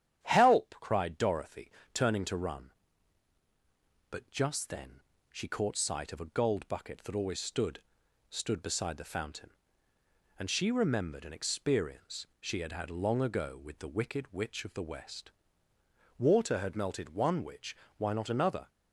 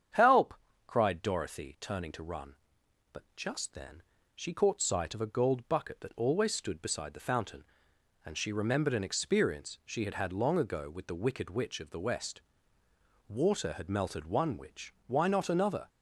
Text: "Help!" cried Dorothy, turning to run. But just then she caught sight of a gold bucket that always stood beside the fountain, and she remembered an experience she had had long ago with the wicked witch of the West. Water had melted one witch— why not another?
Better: second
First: starts louder than the rest; strong; until 1.2 s; 10 dB // pauses between "then" and "she"; slight; at 5.0 s; 0.32 s long // says "stood" twice; at 8.3 s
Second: starts louder than the rest; strong; until 1.4 s; 8 dB // pauses between "then" and "she"; slight; at 4.0 s; 0.32 s long

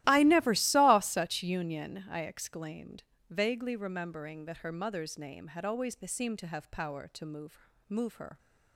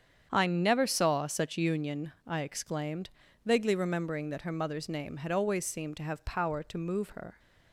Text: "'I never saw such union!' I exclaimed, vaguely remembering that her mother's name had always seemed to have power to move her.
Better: second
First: starts louder than the rest; strong; until 1.0 s; 15.5 dB // says "move" twice; at 7.8 s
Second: starts louder than the rest; strong; until 1.3 s; 8 dB

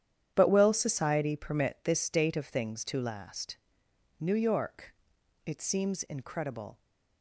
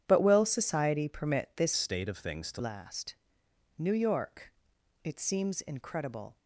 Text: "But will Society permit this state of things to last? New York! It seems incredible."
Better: first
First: starts louder than the rest; strong; until 1.3 s; 10 dB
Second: starts louder than the rest; strong; until 1.0 s; 9.5 dB // changes voice from "state" to "to"; from 1.7 to 2.6 s; 0.9 s long

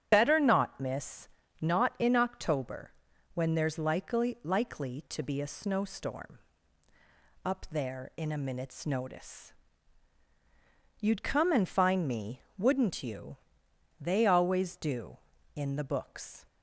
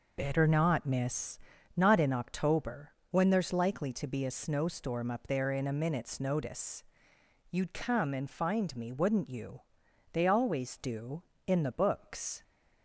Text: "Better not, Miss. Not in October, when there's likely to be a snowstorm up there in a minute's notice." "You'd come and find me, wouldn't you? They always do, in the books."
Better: second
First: starts louder than the rest; strong; until 1.1 s; 8.5 dB // says "likely" twice; at 4.4 s // pauses between "snowstorm" and "up"; at 6.3 s; 1.0 s long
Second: none

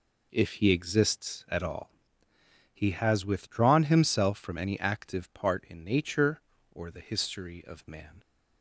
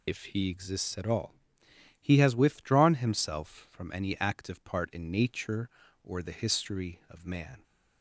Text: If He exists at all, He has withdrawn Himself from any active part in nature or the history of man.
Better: first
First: none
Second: loses the start of "If"; at 0.0 s; 70 ms

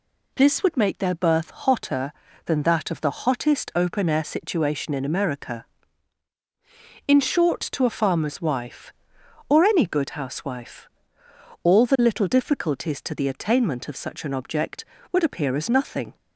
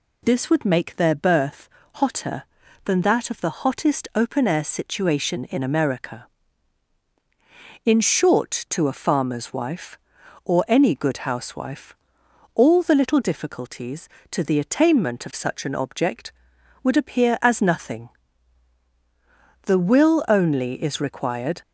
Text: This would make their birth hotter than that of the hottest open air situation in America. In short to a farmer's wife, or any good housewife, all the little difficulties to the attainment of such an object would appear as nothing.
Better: first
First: none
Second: pauses between "birth" and "hotter"; slight; at 1.6 s; 0.28 s long // goes on to say "The will only is required"; strong; from 19.6 s on; 1.9 s long

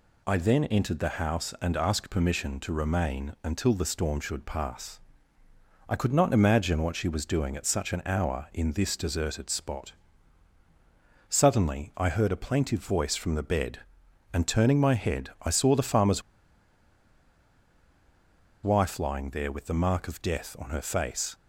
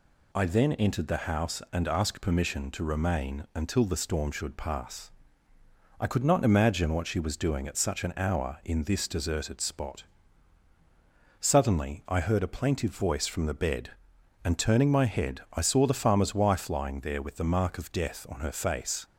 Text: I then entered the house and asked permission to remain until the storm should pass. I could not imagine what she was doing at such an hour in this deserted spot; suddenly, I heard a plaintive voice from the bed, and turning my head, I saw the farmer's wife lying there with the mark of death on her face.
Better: second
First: pauses between "farmer's" and "wife"; strong; at 16.2 s; 2.4 s long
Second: none

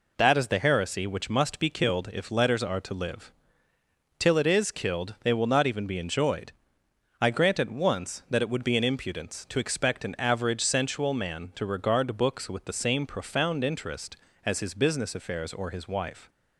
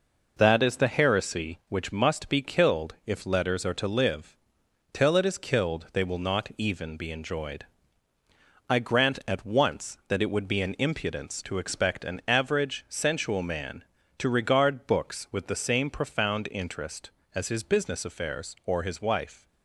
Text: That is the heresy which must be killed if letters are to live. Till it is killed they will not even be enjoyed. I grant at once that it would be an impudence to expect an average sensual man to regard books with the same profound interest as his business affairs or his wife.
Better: neither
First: none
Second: none

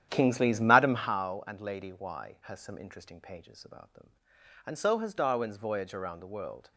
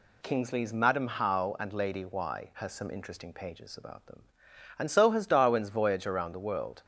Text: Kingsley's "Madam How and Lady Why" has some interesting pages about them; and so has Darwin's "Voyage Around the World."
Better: second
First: starts louder than the rest; strong; until 1.3 s; 10.5 dB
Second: none

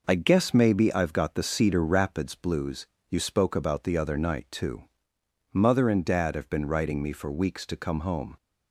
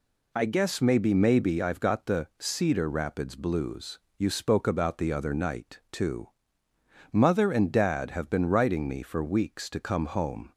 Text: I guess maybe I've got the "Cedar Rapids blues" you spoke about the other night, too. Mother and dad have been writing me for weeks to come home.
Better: first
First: pauses between "blues" and "you"; slight; at 2.8 s; 0.22 s long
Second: says "maybe" twice; at 1.1 s // pauses between "blues" and "you"; slight; at 3.9 s; 0.18 s long

